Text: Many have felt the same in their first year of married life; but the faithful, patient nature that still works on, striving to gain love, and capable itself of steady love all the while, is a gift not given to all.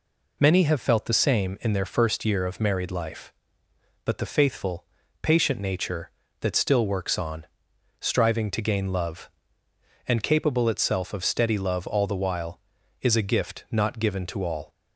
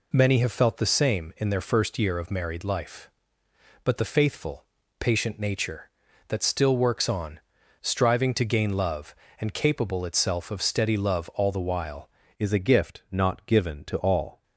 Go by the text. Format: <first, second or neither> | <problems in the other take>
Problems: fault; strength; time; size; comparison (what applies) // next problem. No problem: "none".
first | changes voice at "is"; from 12.4 s on; 2.0 s long